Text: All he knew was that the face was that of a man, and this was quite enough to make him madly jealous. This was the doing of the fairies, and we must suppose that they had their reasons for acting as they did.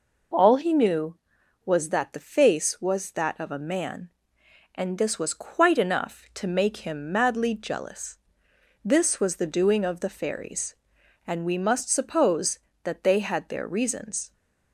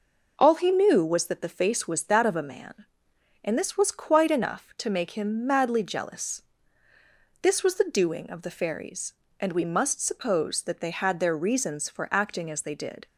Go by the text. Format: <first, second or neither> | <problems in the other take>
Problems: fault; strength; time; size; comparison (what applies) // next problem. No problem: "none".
second | stops before "for acting as they did"; at 14.3 s